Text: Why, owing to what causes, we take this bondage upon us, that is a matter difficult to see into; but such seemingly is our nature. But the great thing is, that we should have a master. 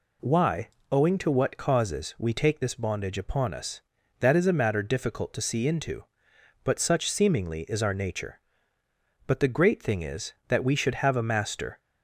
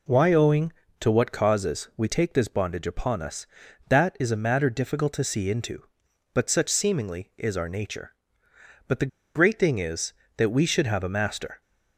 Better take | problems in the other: first | pauses between "the" and "great"; slight; at 9.0 s; 0.26 s long

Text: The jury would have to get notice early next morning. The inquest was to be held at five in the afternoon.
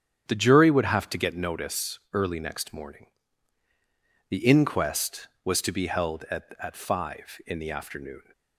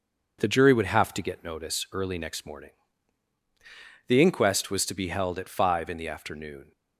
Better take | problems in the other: second | starts louder than the rest; strong; until 1.3 s; 9 dB // says "at" twice; at 6.5 s

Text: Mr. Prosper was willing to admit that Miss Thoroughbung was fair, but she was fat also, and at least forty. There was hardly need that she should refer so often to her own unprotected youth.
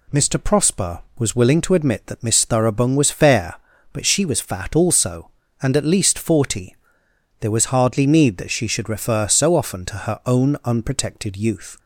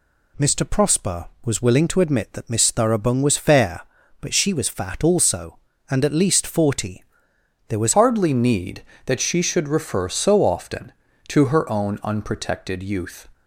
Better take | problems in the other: first | changes voice at "hardly"; from 7.9 s on; 5.3 s long

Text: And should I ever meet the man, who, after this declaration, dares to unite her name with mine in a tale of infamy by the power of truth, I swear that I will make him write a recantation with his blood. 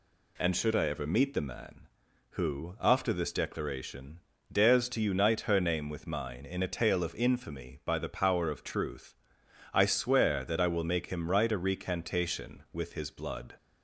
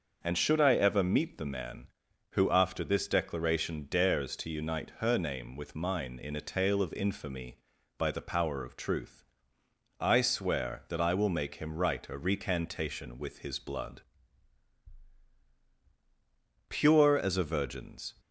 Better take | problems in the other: first | starts louder than the rest; until 1.2 s; 6.5 dB // goes on to say "Pure as a virgin's"; from 16.6 s on; 1.4 s long

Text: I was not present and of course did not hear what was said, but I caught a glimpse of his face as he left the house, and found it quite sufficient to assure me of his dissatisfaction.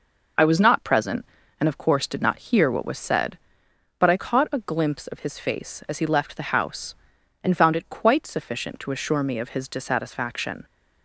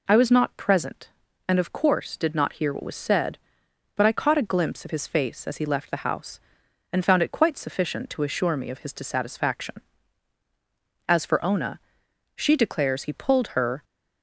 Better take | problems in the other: first | goes on to say "As for Ona she declares he pulled her"; strong; from 11.0 s on; 2.7 s long

